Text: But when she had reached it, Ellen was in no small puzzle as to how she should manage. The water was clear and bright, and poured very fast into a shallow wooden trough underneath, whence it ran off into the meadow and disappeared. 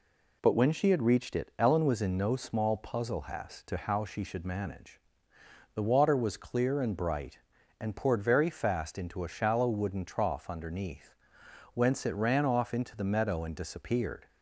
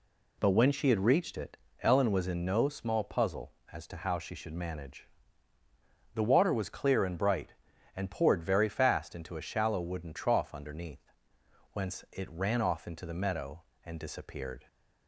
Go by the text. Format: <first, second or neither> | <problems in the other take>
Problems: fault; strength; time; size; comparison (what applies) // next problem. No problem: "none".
second | says "has" for "as"; at 3.2 s